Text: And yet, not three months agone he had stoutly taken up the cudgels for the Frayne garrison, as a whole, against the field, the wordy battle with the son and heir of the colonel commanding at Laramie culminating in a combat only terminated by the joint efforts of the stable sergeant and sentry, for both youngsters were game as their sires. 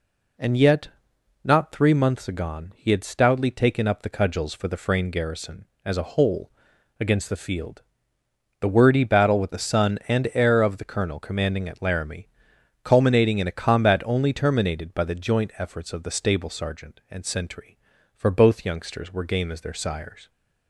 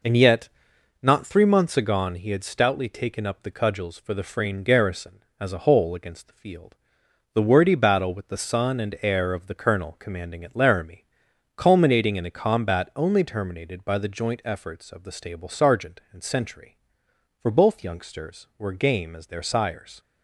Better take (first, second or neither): first